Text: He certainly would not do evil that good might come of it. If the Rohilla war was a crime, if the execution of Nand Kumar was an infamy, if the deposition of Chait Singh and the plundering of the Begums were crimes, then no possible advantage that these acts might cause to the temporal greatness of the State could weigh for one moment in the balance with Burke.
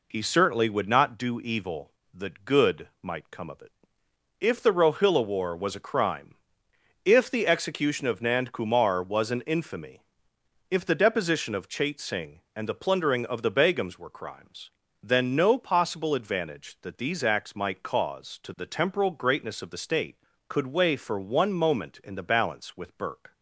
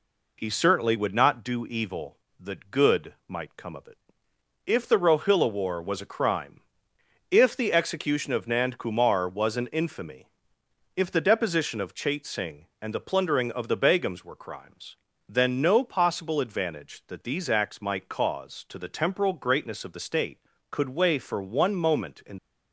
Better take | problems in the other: first | stops before "the balance with Burke"; at 22.3 s

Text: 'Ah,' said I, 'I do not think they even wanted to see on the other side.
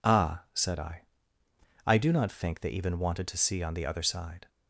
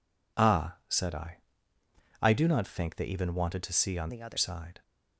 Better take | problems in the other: first | changes voice from "the" to "other"; from 4.0 to 4.3 s; 0.3 s long

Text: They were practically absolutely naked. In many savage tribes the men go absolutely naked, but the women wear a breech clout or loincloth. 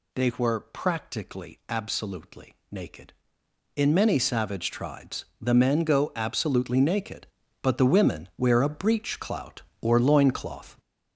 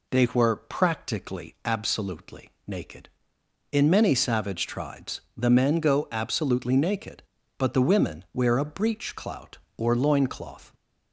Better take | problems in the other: second | gets louder; strong; throughout; 7.5 dB // pauses between "tribes" and "the"; slight; at 5.2 s; 0.16 s long; slight in the second

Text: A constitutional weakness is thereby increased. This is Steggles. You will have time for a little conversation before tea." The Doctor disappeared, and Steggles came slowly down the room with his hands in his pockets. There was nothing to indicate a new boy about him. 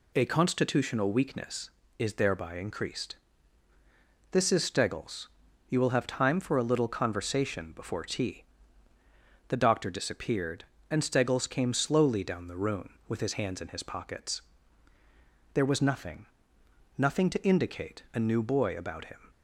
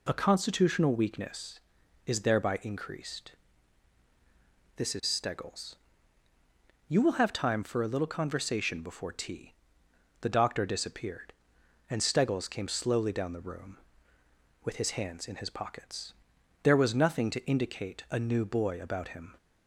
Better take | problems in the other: second | says "nothing" twice; at 16.9 s

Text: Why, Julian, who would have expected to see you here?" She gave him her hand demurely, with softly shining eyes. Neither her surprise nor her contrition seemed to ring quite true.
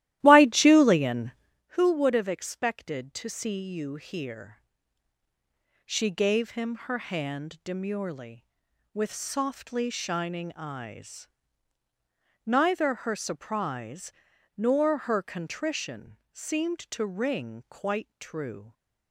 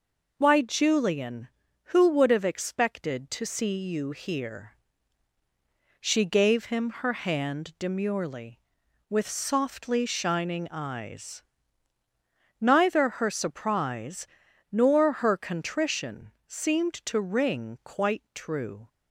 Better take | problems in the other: second | starts louder than the rest; strong; until 1.6 s; 14.5 dB // pauses between "surprise" and "nor"; noticeable; at 14.1 s; 0.46 s long; noticeable in the second // pauses between "contrition" and "seemed"; slight; at 16.1 s; 0.16 s long; slight in the second

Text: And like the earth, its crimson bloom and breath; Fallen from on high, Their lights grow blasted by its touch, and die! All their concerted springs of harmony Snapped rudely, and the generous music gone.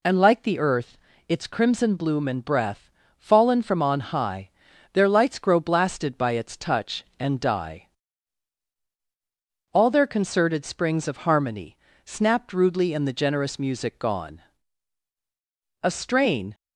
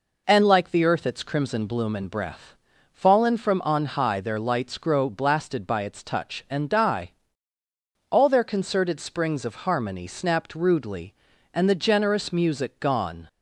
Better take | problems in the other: second | pauses between "harmony" and "Snapped"; slight; at 11.7 s; 0.30 s long // goes on to say "A strain"; noticeable; from 15.8 s on; 0.72 s long

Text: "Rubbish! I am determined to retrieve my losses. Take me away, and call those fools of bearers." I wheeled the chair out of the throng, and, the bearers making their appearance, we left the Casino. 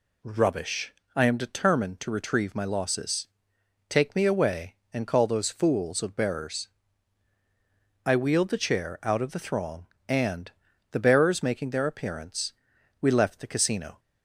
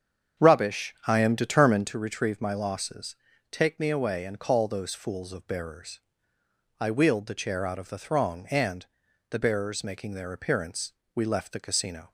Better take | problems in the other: first | starts louder than the rest; strong; until 1.9 s; 7.5 dB

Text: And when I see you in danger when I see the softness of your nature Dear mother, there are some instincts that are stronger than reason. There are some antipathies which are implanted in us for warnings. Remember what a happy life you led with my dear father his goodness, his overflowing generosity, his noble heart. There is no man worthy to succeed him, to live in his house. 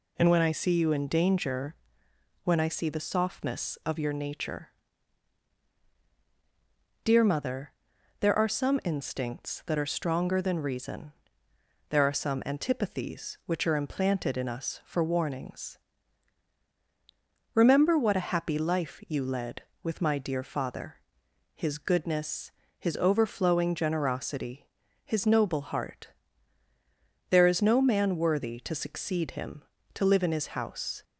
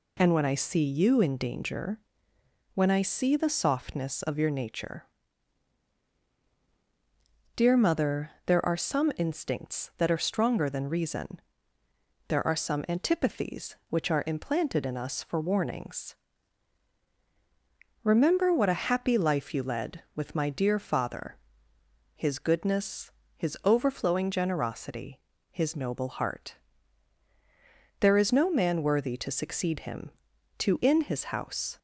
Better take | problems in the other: first | pauses between "danger" and "when"; noticeable; at 1.9 s; 0.74 s long; noticeable in the first // pauses between "nature" and "Dear"; strong; at 5.0 s; 2.5 s long; strong in the first // pauses between "father" and "his"; noticeable; at 21.3 s; 0.78 s long; noticeable in the first // skips "live"; at 30.8 s

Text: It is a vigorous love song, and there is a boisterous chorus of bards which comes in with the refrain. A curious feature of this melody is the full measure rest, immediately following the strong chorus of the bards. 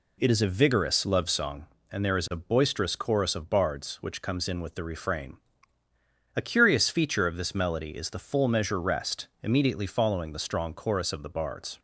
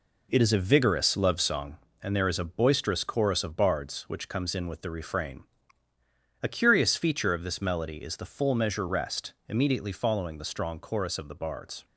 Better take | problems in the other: first | gets quieter; throughout; 6.5 dB

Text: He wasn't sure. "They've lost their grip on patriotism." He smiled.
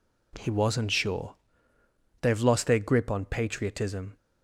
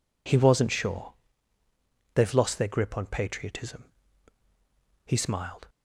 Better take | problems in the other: second | stops before "He smiled"; at 4.1 s

